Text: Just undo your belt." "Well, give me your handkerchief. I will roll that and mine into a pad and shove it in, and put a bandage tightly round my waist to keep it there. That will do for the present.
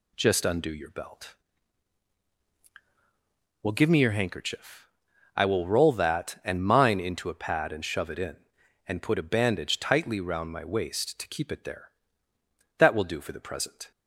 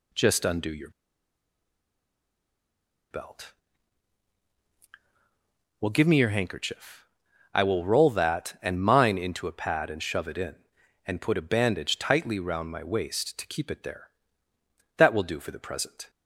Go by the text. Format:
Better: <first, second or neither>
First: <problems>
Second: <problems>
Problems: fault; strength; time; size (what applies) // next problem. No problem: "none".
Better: first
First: none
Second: pauses between "your" and "belt"; strong; at 0.8 s; 2.2 s long